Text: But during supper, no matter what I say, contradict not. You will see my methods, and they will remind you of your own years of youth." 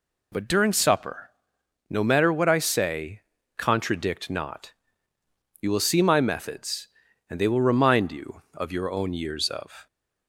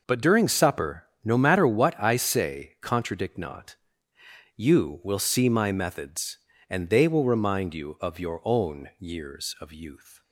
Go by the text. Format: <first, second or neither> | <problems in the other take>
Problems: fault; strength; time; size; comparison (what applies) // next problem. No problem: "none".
second | stops before "youth"; at 9.8 s